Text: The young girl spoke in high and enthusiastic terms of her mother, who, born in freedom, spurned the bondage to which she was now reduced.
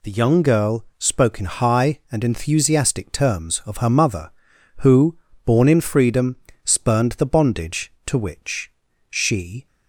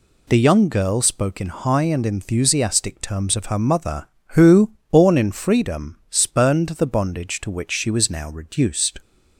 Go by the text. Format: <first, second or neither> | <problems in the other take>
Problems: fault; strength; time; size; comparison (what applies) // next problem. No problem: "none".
second | pauses between "which" and "she"; at 8.7 s; 0.38 s long // stops before "was now reduced"; at 9.6 s